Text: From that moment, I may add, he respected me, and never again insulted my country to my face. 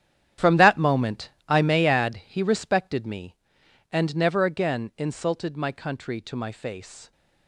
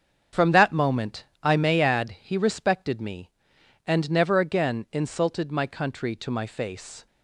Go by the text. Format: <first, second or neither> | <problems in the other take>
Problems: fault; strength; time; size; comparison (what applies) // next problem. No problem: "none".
second | gets quieter; strong; throughout; 14 dB // starts louder than the rest; strong; until 1.5 s; 10 dB; strong in the second